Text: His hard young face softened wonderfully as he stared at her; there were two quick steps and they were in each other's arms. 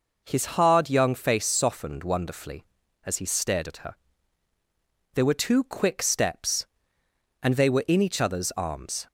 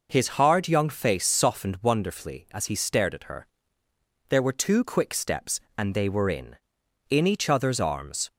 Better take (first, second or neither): first